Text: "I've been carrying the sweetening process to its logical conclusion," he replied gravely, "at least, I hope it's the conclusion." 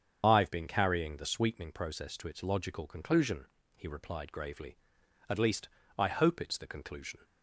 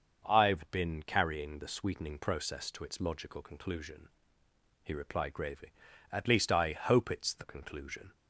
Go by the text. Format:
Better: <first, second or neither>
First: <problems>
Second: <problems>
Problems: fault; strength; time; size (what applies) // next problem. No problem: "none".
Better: second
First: loses the start of "I've"; at 0.2 s; 60 ms // starts louder than the rest; strong; until 1.2 s; 7.5 dB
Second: starts louder than the rest; until 1.2 s; 6.5 dB